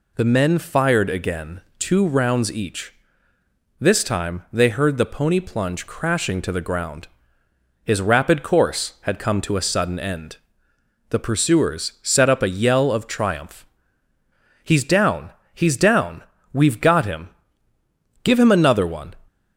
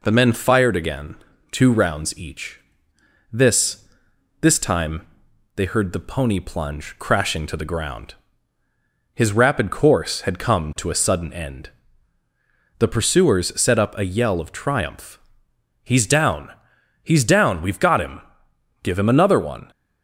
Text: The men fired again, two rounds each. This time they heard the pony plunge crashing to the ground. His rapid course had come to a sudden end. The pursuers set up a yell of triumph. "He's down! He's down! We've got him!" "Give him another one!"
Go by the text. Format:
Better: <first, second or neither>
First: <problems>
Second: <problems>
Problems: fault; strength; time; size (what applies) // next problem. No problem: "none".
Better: first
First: none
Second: says "This" twice; at 4.4 s // pauses between "time" and "they"; noticeable; at 5.0 s; 0.50 s long